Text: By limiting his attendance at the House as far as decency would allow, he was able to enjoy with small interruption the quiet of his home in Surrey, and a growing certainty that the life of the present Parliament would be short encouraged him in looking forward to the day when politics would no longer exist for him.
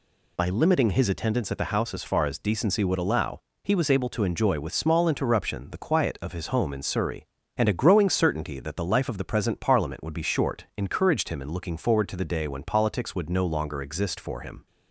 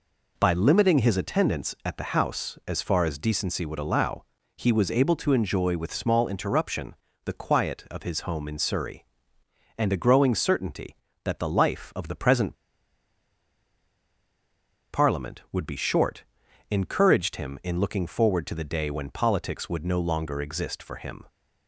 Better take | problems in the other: first | pauses between "interruption" and "the"; slight; at 6.9 s; 0.28 s long // pauses between "present" and "Parliament"; strong; at 12.5 s; 2.3 s long // pauses between "short" and "encouraged"; noticeable; at 16.2 s; 0.48 s long

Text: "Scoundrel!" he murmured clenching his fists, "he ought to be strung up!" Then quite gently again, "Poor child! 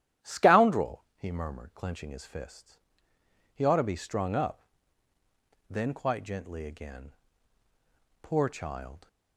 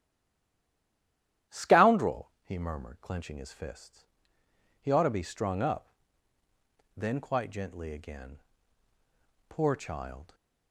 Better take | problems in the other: first | stays silent before the first word; noticeable; until 1.5 s; 1.5 s long // starts louder than the rest; strong; until 2.6 s; 11.5 dB; strong in the first

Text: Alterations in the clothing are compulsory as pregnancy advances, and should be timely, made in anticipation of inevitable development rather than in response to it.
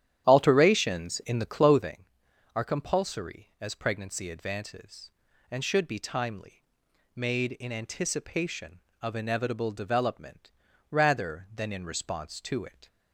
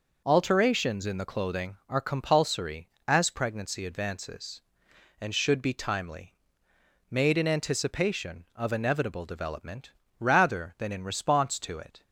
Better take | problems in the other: second | starts louder than the rest; strong; until 1.9 s; 10.5 dB // pauses between "development" and "rather"; at 10.5 s; 0.40 s long; slight in the second

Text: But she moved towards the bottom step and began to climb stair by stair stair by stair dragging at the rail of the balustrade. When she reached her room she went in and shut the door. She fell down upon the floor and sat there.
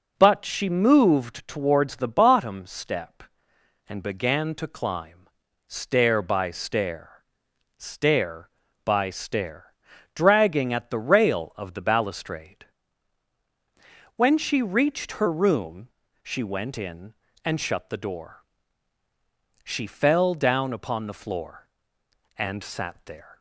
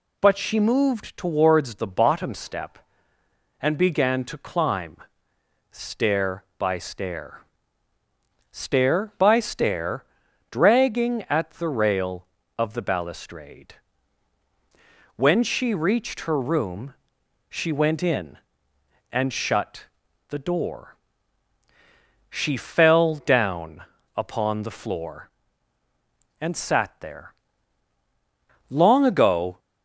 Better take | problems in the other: first | pauses between "climb" and "stair"; noticeable; at 4.9 s; 0.72 s long; also in the first // pauses between "stair" and "stair"; at 7.4 s; 1.0 s long; noticeable in the first // pauses between "stair" and "dragging"; noticeable; at 10.0 s; 0.46 s long; also in the first // pauses between "room" and "she"; noticeable; at 16.9 s; 0.54 s long; slight in the first // pauses between "shut" and "the"; at 19.8 s; 0.44 s long // pauses between "down" and "upon"; slight; at 23.8 s; 0.32 s long // goes on to say "Long ago"; noticeable; from 28.7 s on; 0.88 s long

